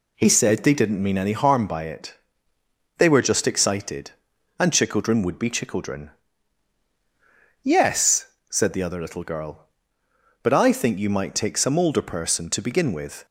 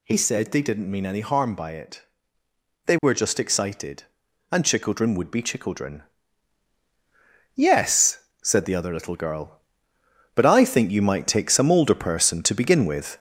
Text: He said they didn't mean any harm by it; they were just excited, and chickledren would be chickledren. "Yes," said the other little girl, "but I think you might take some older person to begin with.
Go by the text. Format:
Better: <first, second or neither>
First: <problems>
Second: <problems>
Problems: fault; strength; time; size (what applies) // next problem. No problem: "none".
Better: first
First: none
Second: gets louder; noticeable; throughout; 5 dB